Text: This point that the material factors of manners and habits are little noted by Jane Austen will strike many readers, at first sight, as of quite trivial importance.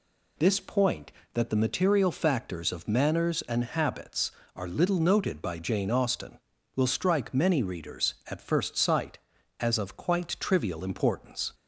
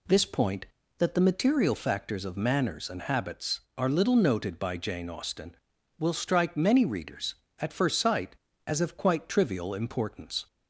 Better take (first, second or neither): neither